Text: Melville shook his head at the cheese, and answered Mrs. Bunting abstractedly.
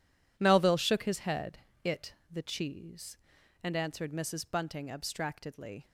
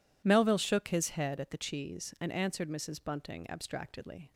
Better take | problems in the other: second | says "it" for "at"; at 1.8 s

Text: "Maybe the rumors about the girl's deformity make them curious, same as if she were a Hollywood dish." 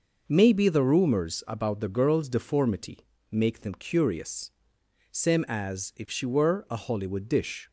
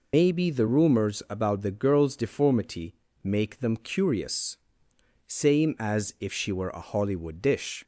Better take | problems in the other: first | loses the start of "Maybe"; at 0.1 s; 115 ms // pauses between "deformity" and "make"; slight; at 2.9 s; 0.26 s long; slight in the first

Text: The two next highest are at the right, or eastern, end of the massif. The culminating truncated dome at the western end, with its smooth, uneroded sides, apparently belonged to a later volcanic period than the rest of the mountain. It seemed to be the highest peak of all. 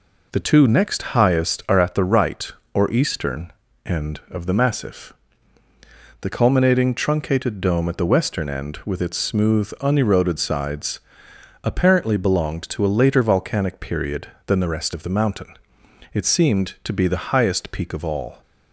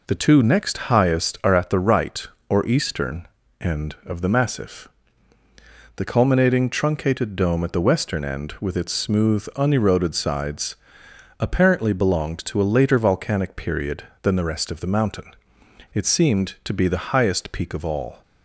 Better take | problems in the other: neither | none

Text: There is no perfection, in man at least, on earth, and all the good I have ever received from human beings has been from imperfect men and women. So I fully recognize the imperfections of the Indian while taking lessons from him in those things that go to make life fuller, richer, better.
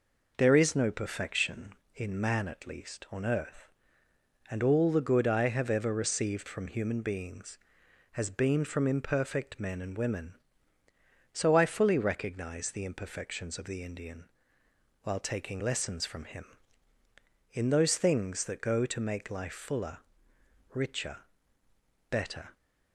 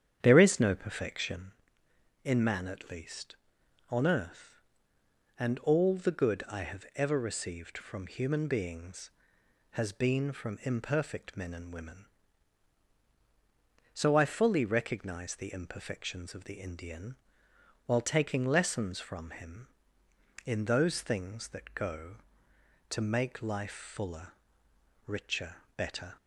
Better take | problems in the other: first | starts louder than the rest; strong; until 1.6 s; 9 dB // pauses between "Indian" and "while"; noticeable; at 17.1 s; 0.72 s long; noticeable in the first

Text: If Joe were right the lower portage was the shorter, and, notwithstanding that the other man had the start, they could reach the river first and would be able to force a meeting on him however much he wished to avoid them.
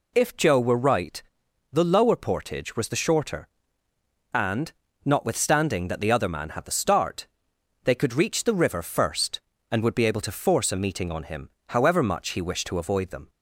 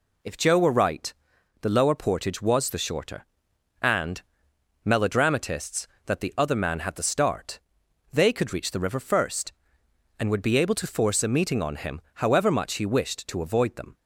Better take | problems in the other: first | pauses between "right" and "the"; noticeable; at 1.1 s; 0.48 s long; noticeable in the first // says "melodramatists" for "notwithstanding"; at 4.8 s // pauses between "him" and "however"; slight; at 11.9 s; 0.16 s long; slight in the first

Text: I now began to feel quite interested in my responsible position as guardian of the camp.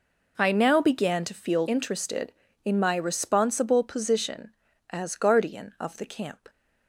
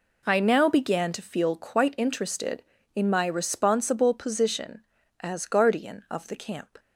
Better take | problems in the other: second | skips "quite"; at 1.6 s

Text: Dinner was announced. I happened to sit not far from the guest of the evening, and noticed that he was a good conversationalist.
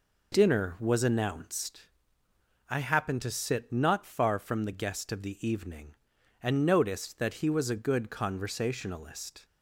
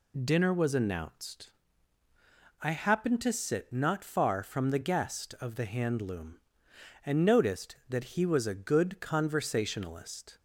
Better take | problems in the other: first | says "handloom" for "evening"; at 5.6 s

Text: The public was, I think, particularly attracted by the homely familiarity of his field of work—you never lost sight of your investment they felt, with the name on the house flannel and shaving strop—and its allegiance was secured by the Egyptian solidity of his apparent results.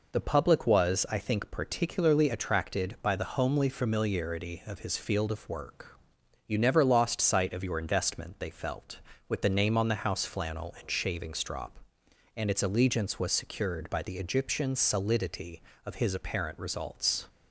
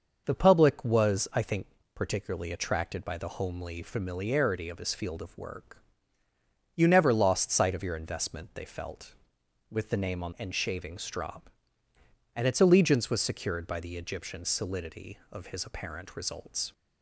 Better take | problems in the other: first | starts louder than the rest; noticeable; until 1.2 s; 6 dB // skips "the house flannel"; at 10.3 s

